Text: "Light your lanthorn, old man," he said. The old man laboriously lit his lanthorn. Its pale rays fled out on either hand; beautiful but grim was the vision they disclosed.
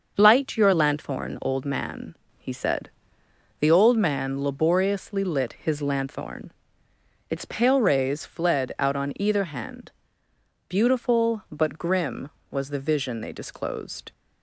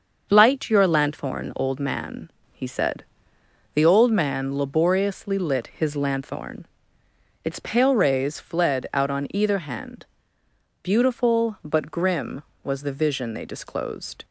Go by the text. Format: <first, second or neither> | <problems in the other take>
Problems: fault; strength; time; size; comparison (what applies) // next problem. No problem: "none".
neither | starts louder than the rest; the same in both